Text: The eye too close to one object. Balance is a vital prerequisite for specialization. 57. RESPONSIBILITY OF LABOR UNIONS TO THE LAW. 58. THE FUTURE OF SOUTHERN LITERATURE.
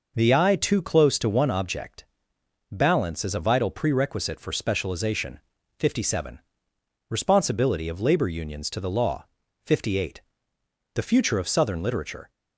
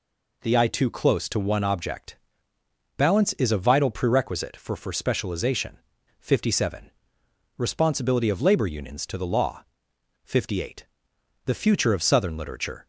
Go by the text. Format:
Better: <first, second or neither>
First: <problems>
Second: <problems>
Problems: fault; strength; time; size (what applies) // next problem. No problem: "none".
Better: first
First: none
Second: says "for" twice; at 4.7 s